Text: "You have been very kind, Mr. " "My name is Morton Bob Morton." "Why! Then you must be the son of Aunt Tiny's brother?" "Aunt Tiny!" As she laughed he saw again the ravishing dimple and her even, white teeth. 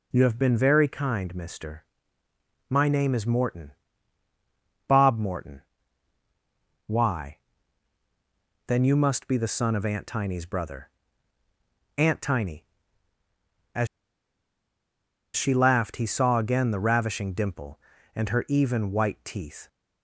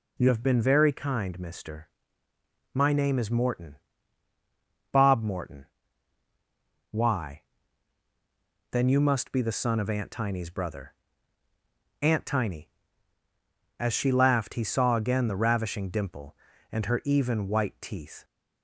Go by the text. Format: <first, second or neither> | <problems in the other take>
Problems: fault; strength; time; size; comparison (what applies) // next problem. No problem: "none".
second | pauses between "Morton" and "Bob"; at 3.7 s; 1.1 s long; also in the second // pauses between "As" and "she"; strong; at 13.8 s; 1.4 s long